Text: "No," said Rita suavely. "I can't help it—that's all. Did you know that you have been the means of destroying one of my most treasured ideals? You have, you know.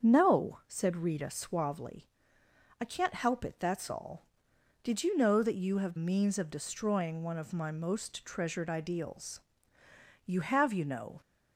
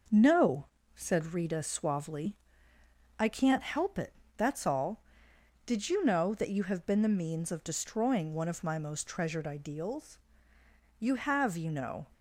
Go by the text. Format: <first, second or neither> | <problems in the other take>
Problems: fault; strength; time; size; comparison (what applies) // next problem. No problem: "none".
second | starts louder than the rest; strong; until 1.0 s; 7.5 dB // skips "been the"; at 5.9 s